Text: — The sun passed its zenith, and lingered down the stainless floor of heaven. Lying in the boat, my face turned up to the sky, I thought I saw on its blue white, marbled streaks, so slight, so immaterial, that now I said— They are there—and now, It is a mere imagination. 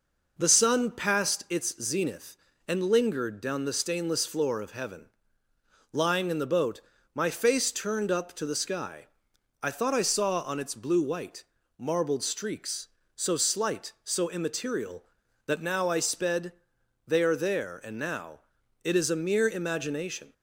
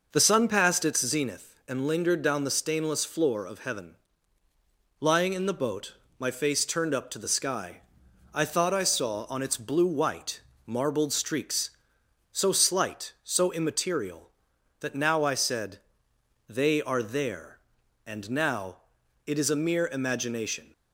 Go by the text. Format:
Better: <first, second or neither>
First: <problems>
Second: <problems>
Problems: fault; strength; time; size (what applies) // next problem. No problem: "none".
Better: second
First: says "sped" for "said"; at 16.0 s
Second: none